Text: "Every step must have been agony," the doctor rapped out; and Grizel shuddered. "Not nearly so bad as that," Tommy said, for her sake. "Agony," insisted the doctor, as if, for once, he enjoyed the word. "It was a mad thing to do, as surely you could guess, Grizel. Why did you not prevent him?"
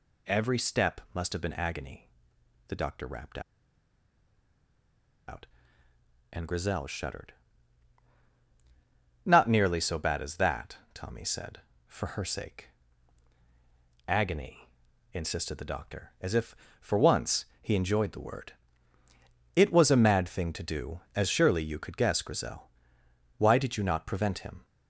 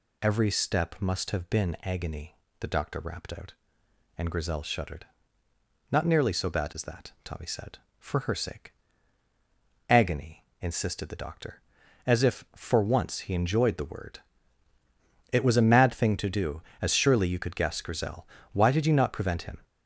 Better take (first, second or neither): second